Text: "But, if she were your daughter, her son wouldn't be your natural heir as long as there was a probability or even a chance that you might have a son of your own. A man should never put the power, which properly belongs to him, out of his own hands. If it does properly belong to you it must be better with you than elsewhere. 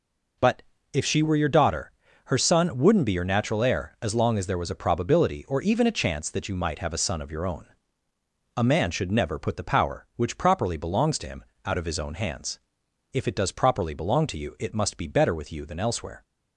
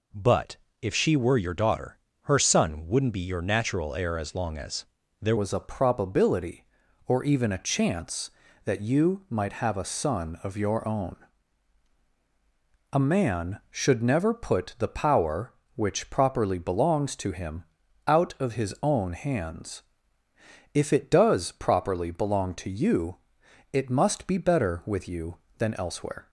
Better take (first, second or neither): first